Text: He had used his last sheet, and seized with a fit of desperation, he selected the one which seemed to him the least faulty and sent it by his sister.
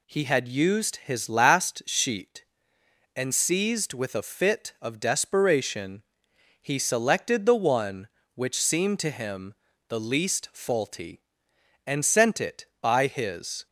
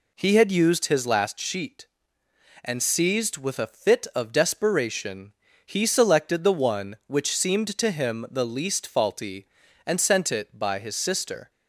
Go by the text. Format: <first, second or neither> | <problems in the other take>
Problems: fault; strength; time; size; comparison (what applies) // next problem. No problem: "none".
second | pauses between "him" and "the"; slight; at 9.5 s; 0.34 s long // stops before "sister"; at 13.6 s